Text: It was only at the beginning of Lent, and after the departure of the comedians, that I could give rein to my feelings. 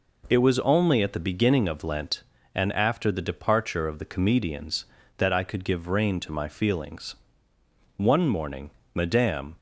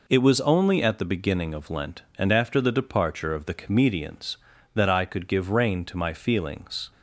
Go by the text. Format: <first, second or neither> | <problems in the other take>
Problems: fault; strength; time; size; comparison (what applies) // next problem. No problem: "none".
second | goes on to say "One morning Madame"; from 7.9 s on; 1.6 s long